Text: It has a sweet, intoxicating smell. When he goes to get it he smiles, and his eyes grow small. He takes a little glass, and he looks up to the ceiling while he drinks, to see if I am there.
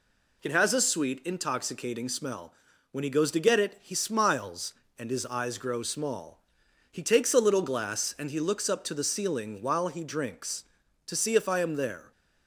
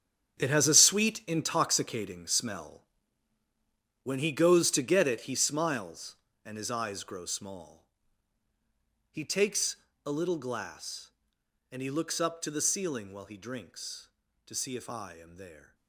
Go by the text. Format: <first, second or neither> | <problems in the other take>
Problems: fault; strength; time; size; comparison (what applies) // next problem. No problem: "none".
first | gets quieter; strong; throughout; 13 dB // pauses between "takes" and "a"; slight; at 9.7 s; 0.30 s long